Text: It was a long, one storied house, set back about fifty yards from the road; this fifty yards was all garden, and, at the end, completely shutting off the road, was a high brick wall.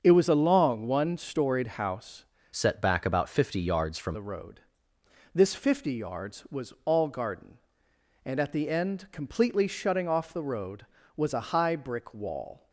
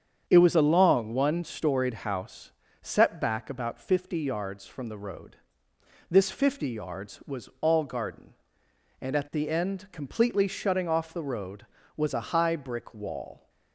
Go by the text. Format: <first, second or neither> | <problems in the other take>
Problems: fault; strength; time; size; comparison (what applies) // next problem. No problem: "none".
second | starts louder than the rest; until 1.0 s; 7 dB; strong in the second // changes voice from "set" to "from"; from 2.5 to 4.1 s; 1.6 s long